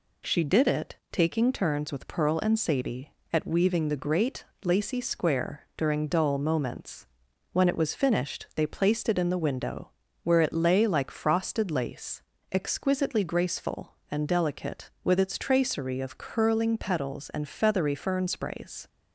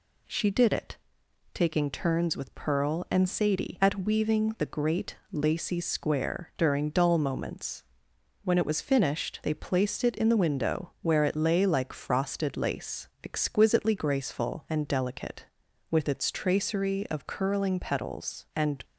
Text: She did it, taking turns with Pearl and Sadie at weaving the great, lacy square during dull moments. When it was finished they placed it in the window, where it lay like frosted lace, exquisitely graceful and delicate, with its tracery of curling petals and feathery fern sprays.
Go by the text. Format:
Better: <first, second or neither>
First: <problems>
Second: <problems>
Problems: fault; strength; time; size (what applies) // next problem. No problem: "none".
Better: first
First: none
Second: stops before "feathery fern sprays"; at 18.8 s